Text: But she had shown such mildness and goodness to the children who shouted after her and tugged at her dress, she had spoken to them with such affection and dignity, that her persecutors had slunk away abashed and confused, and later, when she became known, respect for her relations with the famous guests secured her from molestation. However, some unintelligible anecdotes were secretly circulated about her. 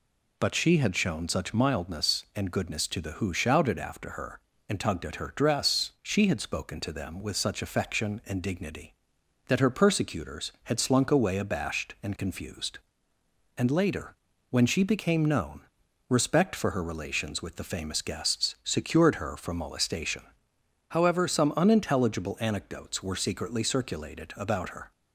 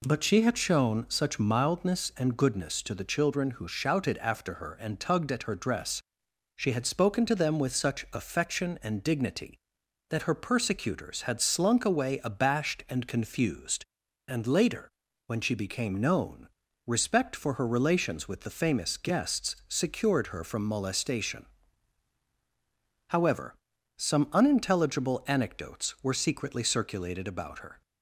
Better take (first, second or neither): second